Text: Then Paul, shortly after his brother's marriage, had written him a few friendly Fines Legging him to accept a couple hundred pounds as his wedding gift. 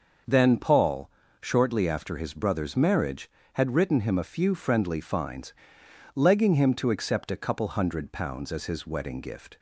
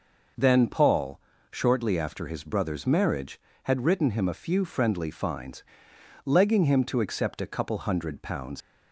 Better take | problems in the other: first | pauses between "Fines" and "Legging"; noticeable; at 5.6 s; 0.64 s long; noticeable in the first // stops before "as his wedding gift"; at 8.6 s

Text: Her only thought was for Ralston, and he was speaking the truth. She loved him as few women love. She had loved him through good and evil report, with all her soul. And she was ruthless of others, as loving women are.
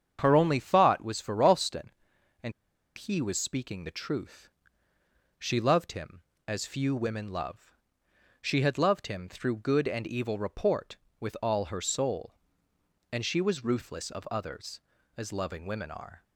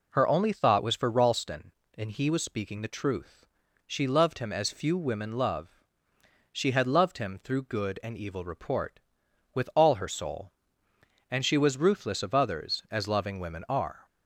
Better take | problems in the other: second | starts louder than the rest; strong; until 1.2 s; 8 dB // pauses between "and" and "he"; at 2.5 s; 0.45 s long

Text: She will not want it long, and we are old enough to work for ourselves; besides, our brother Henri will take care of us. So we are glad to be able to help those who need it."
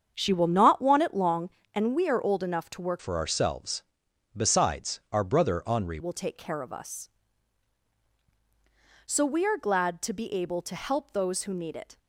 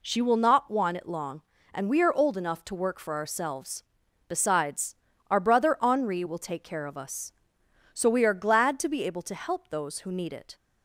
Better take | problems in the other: second | starts louder than the rest; strong; until 1.1 s; 7.5 dB // changes voice from "for" to "Henri"; from 3.0 to 5.9 s; 2.9 s long

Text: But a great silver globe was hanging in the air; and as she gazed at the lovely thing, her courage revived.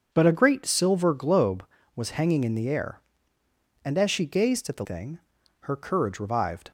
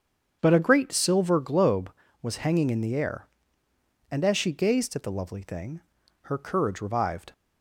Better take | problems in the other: second | starts louder than the rest; until 1.1 s; 6.5 dB; strong in the second // skips "lovely"; at 4.8 s

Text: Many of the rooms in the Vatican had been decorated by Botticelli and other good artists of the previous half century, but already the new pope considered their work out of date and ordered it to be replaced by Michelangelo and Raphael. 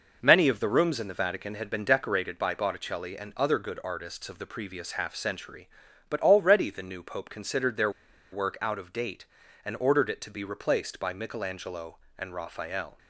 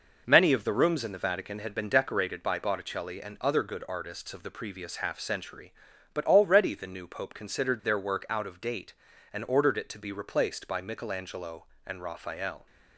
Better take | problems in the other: second | pauses between "their" and "work"; at 7.9 s; 0.42 s long

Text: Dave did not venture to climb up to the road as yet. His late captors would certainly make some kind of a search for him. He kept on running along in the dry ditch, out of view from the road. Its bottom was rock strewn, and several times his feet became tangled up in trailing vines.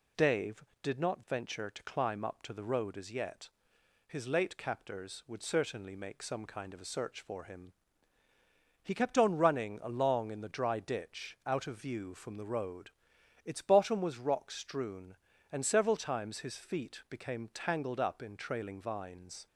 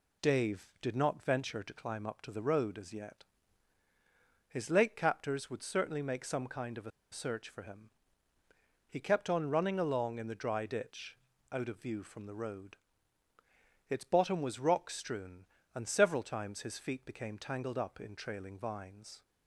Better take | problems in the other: first | pauses between "a" and "search"; slight; at 6.9 s; 0.21 s long

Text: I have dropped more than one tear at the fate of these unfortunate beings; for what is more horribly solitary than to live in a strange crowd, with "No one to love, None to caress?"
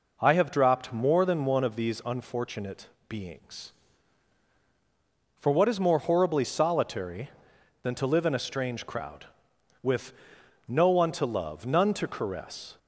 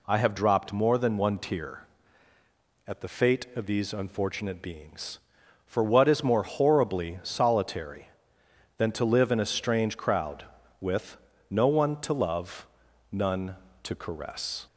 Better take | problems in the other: second | skips "tear at the fate"; at 1.6 s // pauses between "unfortunate" and "beings"; slight; at 2.8 s; 0.20 s long // pauses between "with" and "No"; noticeable; at 10.1 s; 0.54 s long; slight in the second

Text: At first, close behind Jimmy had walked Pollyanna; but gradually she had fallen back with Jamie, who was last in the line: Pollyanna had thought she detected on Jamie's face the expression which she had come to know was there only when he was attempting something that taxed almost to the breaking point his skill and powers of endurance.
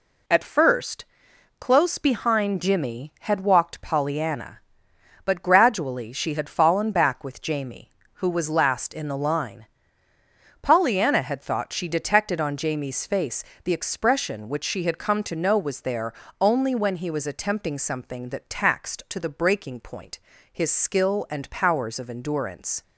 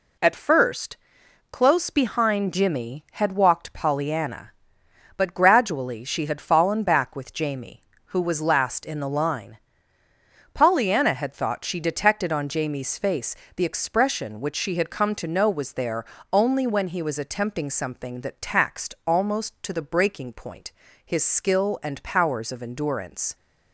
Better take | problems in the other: second | pauses between "face" and "the"; slight; at 13.4 s; 0.22 s long; slight in the second // pauses between "there" and "only"; slight; at 16.1 s; 0.28 s long; slight in the second // skips "almost"; at 19.0 s // pauses between "point" and "his"; slight; at 20.1 s; 0.34 s long; slight in the second

